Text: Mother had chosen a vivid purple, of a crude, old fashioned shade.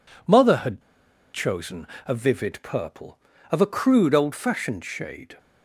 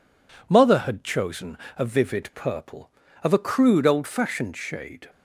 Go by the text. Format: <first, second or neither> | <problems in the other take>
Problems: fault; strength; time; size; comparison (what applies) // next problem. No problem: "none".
second | pauses between "had" and "chosen"; noticeable; at 0.8 s; 0.52 s long // pauses between "chosen" and "a"; slight; at 1.8 s; 0.18 s long; slight in the second